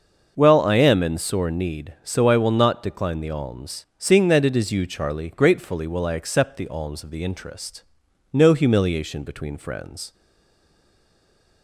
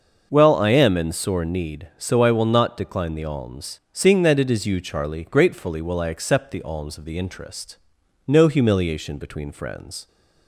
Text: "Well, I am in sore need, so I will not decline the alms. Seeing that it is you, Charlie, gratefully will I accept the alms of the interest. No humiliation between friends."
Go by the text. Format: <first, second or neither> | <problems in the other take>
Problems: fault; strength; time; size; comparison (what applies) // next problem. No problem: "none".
second | starts louder than the rest; noticeable; until 1.3 s; 6 dB; noticeable in the second // stays silent after the last word; noticeable; from 10.1 s on; 1.5 s long